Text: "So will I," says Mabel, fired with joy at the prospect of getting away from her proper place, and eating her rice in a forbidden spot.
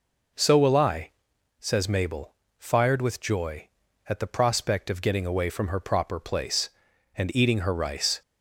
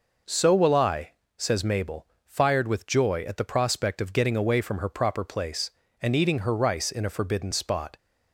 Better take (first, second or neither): second